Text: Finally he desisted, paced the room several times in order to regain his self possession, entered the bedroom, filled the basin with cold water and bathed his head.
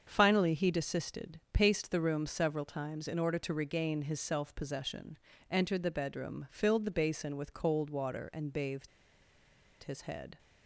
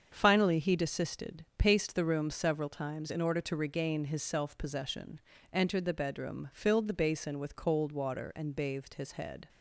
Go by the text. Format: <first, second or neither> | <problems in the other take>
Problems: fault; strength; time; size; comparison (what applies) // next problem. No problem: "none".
second | starts louder than the rest; until 1.0 s; 7 dB; also in the second // pauses between "bathed" and "his"; noticeable; at 8.8 s; 0.95 s long